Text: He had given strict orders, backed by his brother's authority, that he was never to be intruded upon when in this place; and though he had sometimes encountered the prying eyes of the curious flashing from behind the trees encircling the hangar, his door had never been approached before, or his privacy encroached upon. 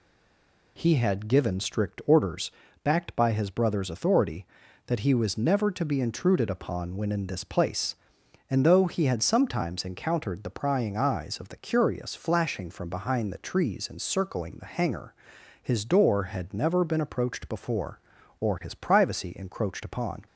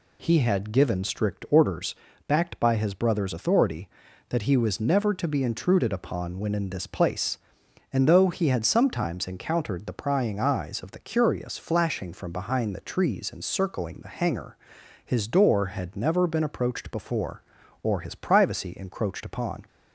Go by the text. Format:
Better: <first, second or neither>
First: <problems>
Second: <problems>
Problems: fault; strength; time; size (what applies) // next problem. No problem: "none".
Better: second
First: stays silent before the first word; slight; until 0.7 s; 0.7 s long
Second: none